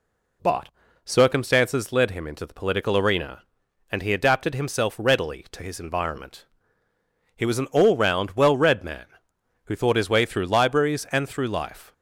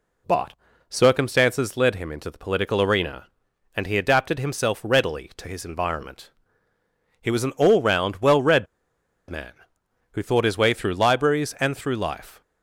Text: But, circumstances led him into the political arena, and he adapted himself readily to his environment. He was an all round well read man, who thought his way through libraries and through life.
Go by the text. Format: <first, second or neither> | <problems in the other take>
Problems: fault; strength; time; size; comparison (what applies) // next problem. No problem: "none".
first | pauses between "read" and "man"; noticeable; at 8.6 s; 0.64 s long